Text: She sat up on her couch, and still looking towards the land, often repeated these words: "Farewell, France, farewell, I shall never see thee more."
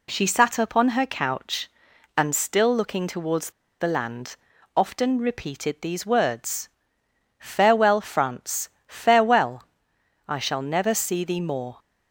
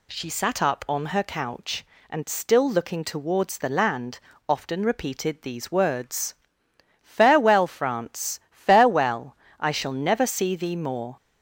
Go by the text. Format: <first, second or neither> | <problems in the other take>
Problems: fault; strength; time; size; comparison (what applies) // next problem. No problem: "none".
second | pauses between "towards" and "the"; slight; at 3.5 s; 0.29 s long